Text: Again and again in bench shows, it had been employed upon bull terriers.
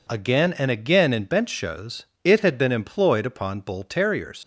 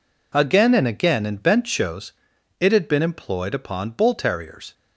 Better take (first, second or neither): second